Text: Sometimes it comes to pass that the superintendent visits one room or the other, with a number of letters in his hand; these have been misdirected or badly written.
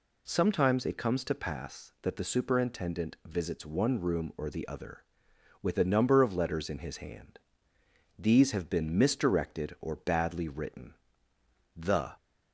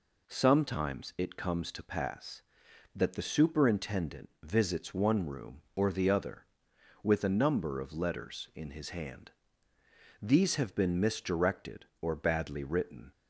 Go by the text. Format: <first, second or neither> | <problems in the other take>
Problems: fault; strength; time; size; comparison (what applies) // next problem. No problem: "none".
second | goes on to say "The"; slight; from 11.7 s on; 0.40 s long